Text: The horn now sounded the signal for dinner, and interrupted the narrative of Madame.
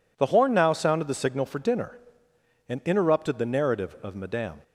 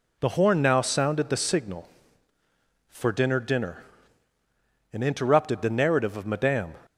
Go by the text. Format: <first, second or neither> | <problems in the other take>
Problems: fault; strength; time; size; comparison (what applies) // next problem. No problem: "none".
first | says "dinner" twice; at 3.3 s